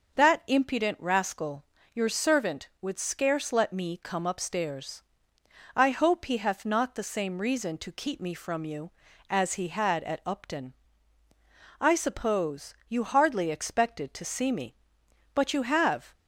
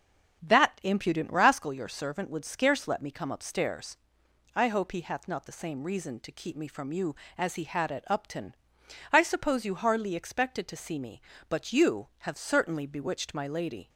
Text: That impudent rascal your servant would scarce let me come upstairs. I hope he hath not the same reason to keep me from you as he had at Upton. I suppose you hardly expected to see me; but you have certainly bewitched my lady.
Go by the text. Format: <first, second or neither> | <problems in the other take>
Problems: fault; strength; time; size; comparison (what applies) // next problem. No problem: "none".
second | starts louder than the rest; until 1.2 s; 6.5 dB; strong in the second // pauses between "rascal" and "your"; slight; at 1.6 s; 0.30 s long // stops before "certainly bewitched my lady"; at 16.1 s